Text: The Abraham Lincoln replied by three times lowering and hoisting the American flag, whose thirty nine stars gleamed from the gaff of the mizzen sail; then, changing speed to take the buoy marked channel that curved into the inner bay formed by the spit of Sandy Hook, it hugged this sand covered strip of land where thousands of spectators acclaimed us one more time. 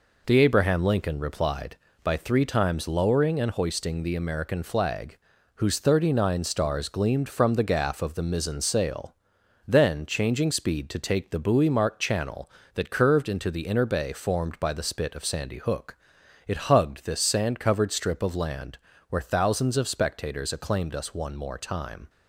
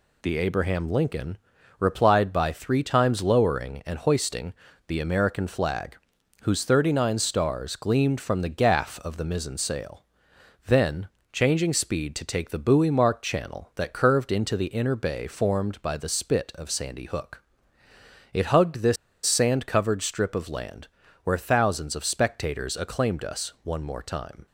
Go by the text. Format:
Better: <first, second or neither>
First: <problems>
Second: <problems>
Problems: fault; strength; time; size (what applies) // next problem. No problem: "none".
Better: first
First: pauses between "land" and "where"; slight; at 18.7 s; 0.32 s long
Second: pauses between "Lincoln" and "replied"; at 1.3 s; 0.42 s long // pauses between "hoisting" and "the"; slight; at 4.5 s; 0.34 s long // pauses between "this" and "sand"; slight; at 18.9 s; 0.30 s long // pauses between "land" and "where"; slight; at 20.8 s; 0.36 s long